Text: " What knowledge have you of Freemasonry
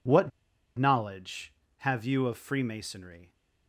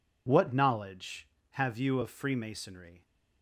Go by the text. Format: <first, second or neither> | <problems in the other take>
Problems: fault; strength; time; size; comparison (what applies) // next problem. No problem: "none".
second | pauses between "What" and "knowledge"; noticeable; at 0.3 s; 0.46 s long